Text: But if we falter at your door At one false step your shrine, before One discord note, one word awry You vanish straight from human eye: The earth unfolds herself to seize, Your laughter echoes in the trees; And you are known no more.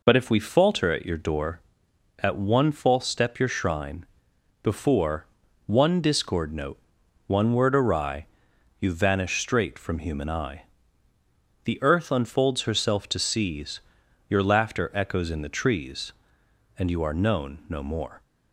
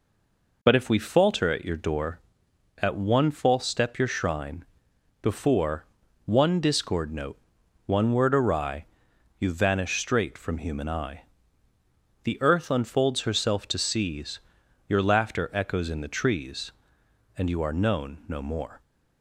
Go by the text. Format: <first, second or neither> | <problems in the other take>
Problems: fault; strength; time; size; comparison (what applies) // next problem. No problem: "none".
first | stays silent before the first word; slight; until 0.6 s; 0.6 s long // pauses between "before" and "One"; at 5.8 s; 0.40 s long; also in the first // pauses between "awry" and "You"; noticeable; at 8.8 s; 0.52 s long; noticeable in the first